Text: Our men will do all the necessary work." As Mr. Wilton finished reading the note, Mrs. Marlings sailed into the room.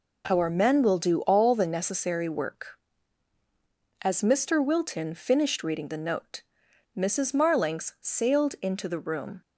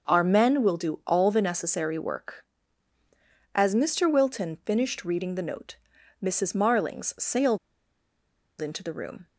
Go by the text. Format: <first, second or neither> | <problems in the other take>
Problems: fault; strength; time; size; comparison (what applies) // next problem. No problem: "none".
first | starts louder than the rest; until 1.1 s; 6.5 dB // pauses between "sailed" and "into"; at 7.5 s; 1.0 s long